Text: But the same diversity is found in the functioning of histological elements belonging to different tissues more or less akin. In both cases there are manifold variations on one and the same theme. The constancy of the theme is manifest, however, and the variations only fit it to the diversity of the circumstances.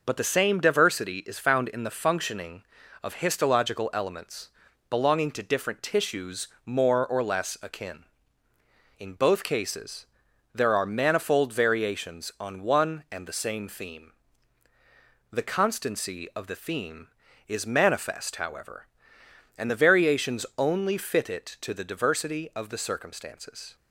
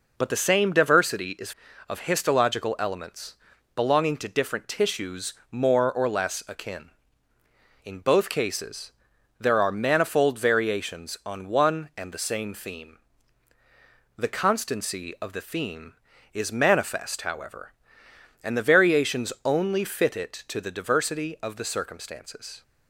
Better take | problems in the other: first | skips "found in the functioning"; at 1.6 s // pauses between "elements" and "belonging"; at 3.3 s; 0.42 s long; also in the first // pauses between "tissues" and "more"; slight; at 5.3 s; 0.18 s long; slight in the first // pauses between "cases" and "there"; noticeable; at 8.9 s; 0.48 s long; noticeable in the first

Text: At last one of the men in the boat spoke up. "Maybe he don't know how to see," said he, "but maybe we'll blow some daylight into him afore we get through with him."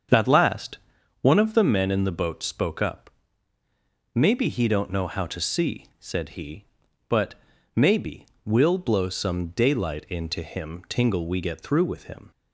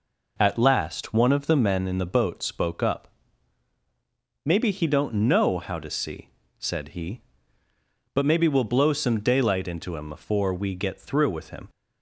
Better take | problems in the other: second | starts louder than the rest; until 1.5 s; 7 dB // pauses between "last" and "one"; at 0.7 s; 0.44 s long // pauses between "but" and "maybe"; at 7.3 s; 0.40 s long // pauses between "maybe" and "we'll"; slight; at 8.2 s; 0.18 s long // says "tingle" for "afore"; at 10.8 s

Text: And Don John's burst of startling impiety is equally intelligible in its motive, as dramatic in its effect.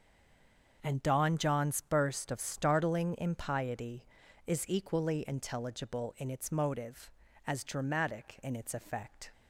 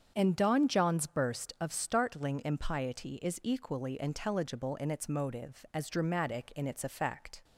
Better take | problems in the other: second | stays silent before the first word; slight; until 0.8 s; 0.8 s long // starts louder than the rest; until 1.8 s; 7 dB; strong in the second

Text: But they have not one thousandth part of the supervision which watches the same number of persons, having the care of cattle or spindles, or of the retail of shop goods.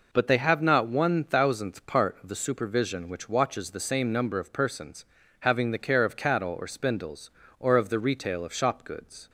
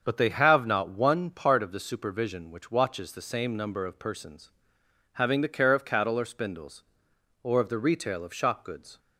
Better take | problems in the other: first | starts louder than the rest; until 1.0 s; 6.5 dB // skips "thousandth"; at 1.3 s

